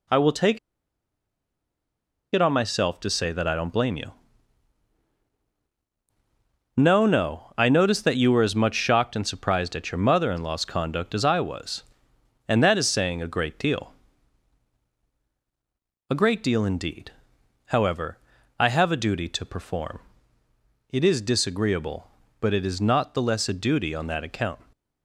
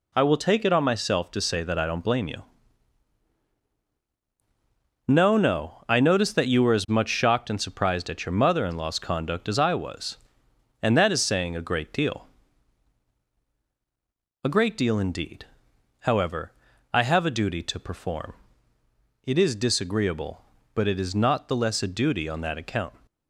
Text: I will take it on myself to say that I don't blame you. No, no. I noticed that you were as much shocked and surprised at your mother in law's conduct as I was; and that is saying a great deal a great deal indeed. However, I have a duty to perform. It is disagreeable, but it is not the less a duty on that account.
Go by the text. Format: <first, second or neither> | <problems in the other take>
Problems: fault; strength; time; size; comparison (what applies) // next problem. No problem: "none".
second | pauses between "take" and "it"; strong; at 0.5 s; 1.7 s long // pauses between "deal" and "a"; strong; at 13.9 s; 2.1 s long; strong in the second